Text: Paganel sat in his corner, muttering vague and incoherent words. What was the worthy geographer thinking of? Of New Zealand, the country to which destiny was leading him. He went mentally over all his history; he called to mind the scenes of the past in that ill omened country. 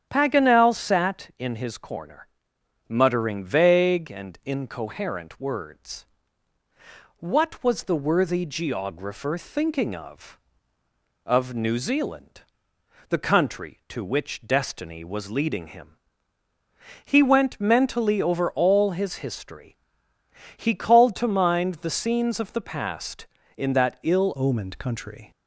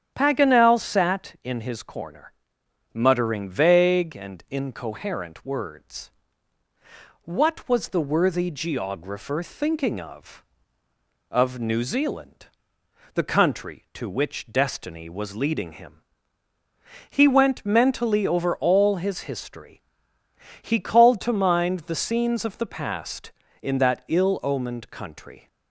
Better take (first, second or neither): second